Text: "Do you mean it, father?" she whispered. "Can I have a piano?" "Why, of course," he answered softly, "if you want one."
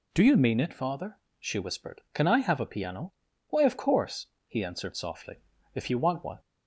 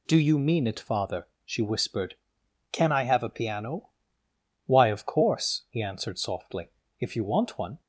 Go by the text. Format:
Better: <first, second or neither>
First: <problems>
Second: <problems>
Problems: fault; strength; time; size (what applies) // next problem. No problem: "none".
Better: neither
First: none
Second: none